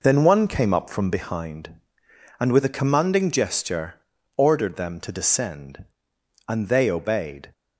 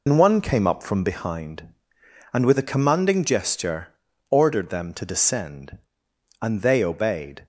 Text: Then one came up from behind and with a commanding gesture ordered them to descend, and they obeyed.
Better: first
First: pauses between "gesture" and "ordered"; at 3.9 s; 0.42 s long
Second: loses the start of "Then"; at 0.0 s; 110 ms // pauses between "gesture" and "ordered"; at 3.8 s; 0.42 s long

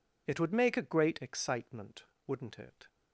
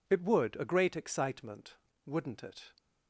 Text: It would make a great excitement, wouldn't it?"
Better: first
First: none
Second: skips "make"; at 0.5 s

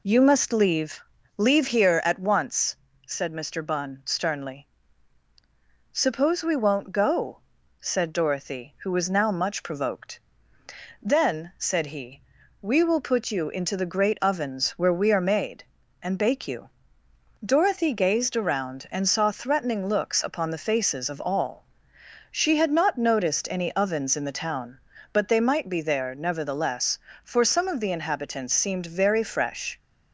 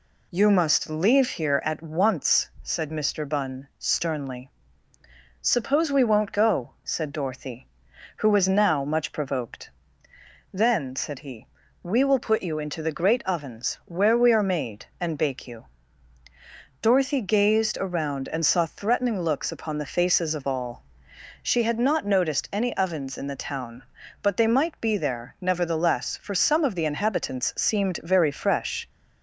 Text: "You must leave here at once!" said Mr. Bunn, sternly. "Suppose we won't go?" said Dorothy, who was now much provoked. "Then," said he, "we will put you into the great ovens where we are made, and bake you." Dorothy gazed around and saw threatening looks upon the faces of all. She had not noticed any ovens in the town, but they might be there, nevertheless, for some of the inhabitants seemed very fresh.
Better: second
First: says "leave" twice; at 1.3 s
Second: none

